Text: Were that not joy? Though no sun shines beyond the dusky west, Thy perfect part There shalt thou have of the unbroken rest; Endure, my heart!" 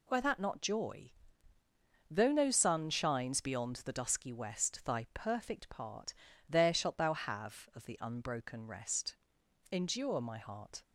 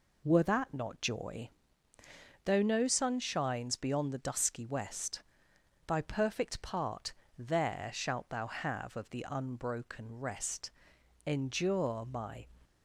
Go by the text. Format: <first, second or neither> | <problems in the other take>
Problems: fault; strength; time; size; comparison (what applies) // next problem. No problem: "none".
first | pauses between "part" and "There"; slight; at 7.1 s; 0.24 s long; slight in the first // stops before "heart"; at 12.6 s